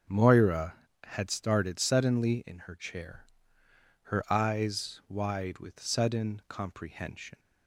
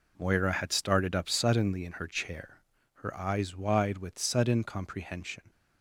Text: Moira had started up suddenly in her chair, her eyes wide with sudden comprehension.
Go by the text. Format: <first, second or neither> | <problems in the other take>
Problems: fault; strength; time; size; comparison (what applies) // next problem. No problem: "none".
second | starts louder than the rest; until 1.3 s; 6.5 dB // skips "up"; at 1.7 s